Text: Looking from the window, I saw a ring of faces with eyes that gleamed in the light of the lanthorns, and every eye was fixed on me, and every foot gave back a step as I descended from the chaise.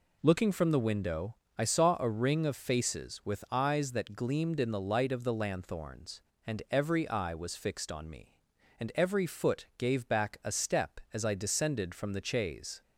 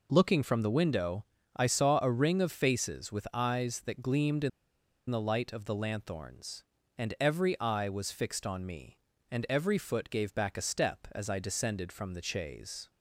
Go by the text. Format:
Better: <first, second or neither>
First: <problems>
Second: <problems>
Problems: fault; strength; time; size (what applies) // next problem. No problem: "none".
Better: first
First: none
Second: pauses between "in" and "the"; noticeable; at 4.4 s; 0.60 s long